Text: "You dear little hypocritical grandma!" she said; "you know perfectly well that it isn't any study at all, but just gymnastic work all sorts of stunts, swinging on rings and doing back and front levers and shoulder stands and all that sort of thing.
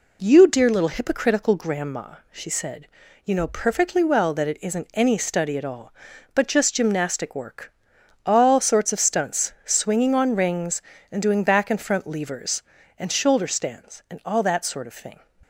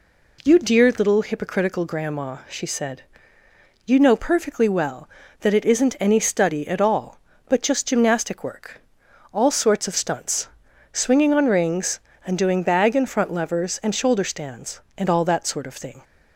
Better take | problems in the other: first | pauses between "work" and "all"; noticeable; at 8.7 s; 0.54 s long; noticeable in the first // says "bag" for "back"; at 12.6 s

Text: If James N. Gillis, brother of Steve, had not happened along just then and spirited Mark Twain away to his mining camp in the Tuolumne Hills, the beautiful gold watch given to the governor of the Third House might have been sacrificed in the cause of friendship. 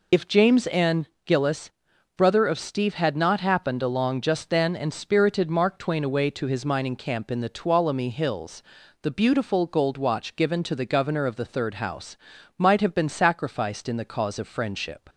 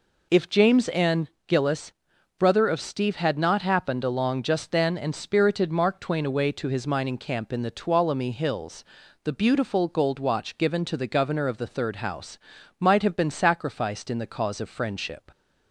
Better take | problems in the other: second | loses the start of "If"; at 0.1 s; 35 ms // pauses between "House" and "might"; at 12.1 s; 0.40 s long; also in the second

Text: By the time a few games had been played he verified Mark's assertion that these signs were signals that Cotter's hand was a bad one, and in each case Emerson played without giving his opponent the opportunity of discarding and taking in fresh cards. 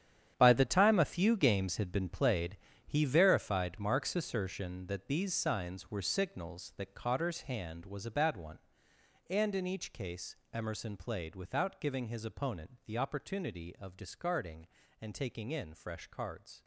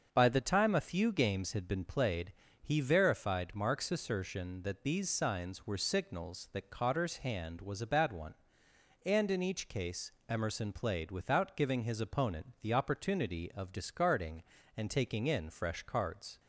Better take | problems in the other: second | gets quieter; strong; throughout; 12.5 dB // starts louder than the rest; strong; until 1.3 s; 9.5 dB; also in the second // pauses between "played" and "he"; slight; at 2.5 s; 0.30 s long; slight in the second // pauses between "case" and "Emerson"; slight; at 10.3 s; 0.16 s long; slight in the second

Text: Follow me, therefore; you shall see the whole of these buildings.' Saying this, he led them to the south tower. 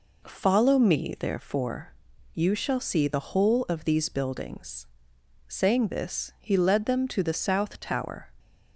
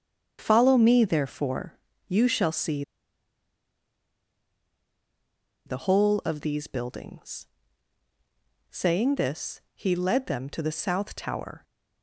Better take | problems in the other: first | starts louder than the rest; strong; until 1.4 s; 7.5 dB // pauses between "see" and "the"; strong; at 2.8 s; 2.8 s long

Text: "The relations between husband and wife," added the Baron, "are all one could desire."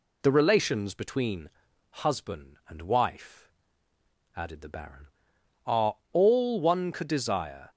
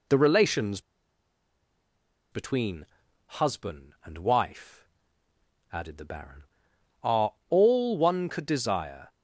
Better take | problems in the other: first | pauses between "relations" and "between"; strong; at 0.7 s; 1.5 s long // pauses between "between" and "husband"; at 2.8 s; 0.40 s long; also in the first // pauses between "are" and "all"; slight; at 7.3 s; 0.16 s long; slight in the first

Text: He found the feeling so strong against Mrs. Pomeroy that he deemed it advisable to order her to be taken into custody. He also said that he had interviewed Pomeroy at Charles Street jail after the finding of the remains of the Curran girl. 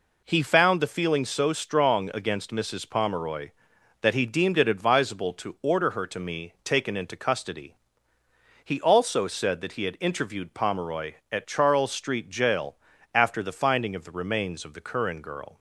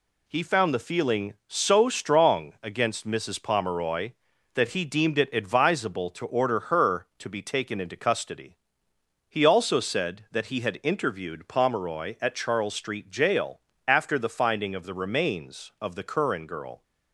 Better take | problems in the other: second | says "me" for "be"; at 6.1 s // pauses between "jail" and "after"; slight; at 12.7 s; 0.36 s long; slight in the second

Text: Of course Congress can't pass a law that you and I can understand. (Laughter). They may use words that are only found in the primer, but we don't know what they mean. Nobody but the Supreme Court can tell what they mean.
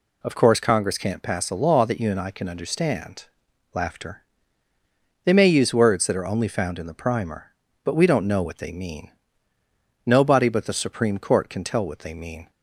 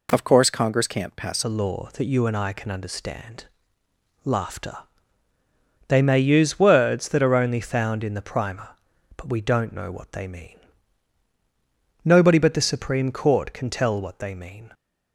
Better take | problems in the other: first | changes voice at "a"; from 1.4 s on; 13.3 s long

